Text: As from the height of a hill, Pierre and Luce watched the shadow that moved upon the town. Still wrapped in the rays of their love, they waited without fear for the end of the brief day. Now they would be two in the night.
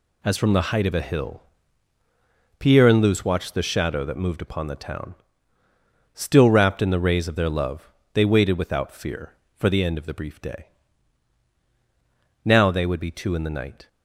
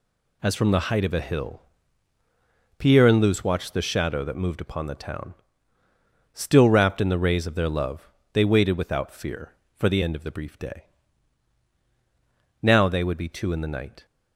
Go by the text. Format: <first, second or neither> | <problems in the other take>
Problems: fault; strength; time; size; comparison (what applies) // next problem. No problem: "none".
neither | none